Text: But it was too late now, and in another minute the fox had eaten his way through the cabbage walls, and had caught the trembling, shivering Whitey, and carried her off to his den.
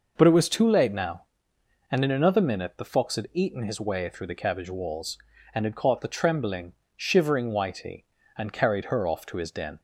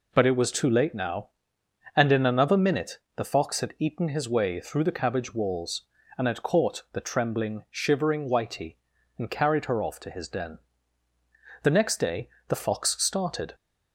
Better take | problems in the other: first | pauses between "minute" and "the"; slight; at 2.9 s; 0.16 s long // goes on to say "The next day the fox started"; strong; from 11.6 s on; 1.9 s long

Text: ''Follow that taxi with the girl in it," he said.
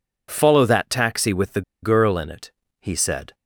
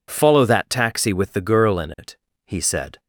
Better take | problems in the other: second | pauses between "the" and "girl"; slight; at 1.6 s; 0.21 s long

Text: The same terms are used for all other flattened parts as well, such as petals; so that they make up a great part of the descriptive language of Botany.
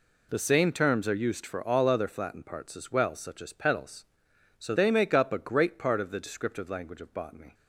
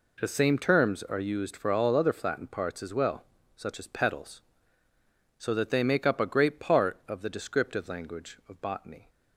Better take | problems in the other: second | skips "that"; at 4.7 s

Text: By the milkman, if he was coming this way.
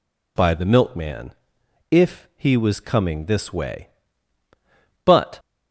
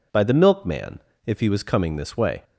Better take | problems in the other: second | goes on to say "But"; slight; from 5.0 s on; 0.36 s long

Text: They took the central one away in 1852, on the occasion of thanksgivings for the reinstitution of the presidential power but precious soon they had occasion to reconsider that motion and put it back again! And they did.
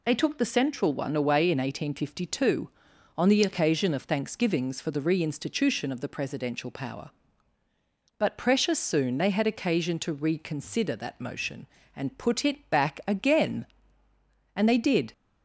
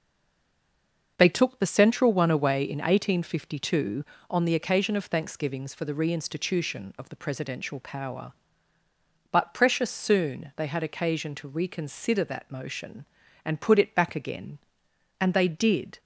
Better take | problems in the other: first | stays silent before the first word; noticeable; until 1.1 s; 1.1 s long // starts louder than the rest; noticeable; until 2.1 s; 6 dB

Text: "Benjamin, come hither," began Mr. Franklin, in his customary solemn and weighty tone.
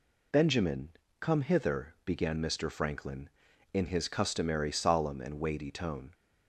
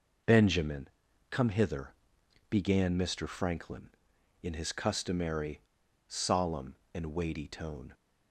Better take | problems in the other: first | pauses between "customary" and "solemn"; noticeable; at 5.5 s; 0.49 s long

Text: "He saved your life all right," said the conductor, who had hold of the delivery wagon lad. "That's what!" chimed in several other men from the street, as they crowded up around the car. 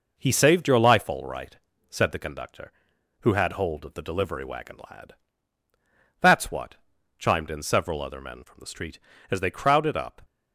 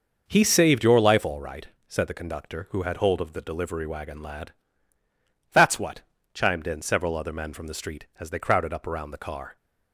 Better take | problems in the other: second | stops before "around the car"; at 10.2 s

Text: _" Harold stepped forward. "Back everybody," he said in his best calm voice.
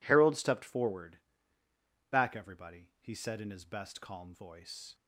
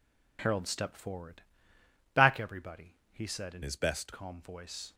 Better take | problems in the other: first | changes voice from "his" to "best"; from 3.6 to 4.1 s; 0.5 s long

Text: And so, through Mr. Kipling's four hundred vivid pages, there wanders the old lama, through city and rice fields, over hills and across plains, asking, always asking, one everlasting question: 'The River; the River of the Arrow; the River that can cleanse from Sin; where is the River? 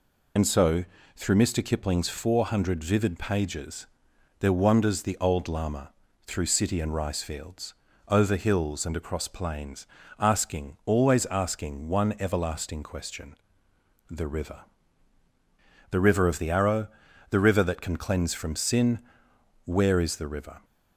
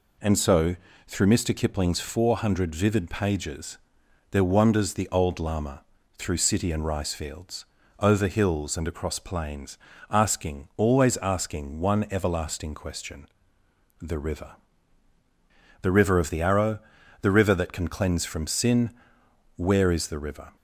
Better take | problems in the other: second | loses the start of "And"; at 0.3 s; 75 ms

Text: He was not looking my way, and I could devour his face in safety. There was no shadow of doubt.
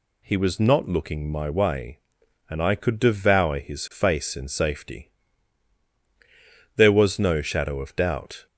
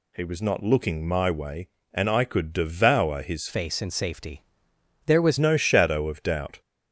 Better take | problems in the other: first | changes voice from "face" to "was"; from 3.4 to 5.3 s; 1.9 s long

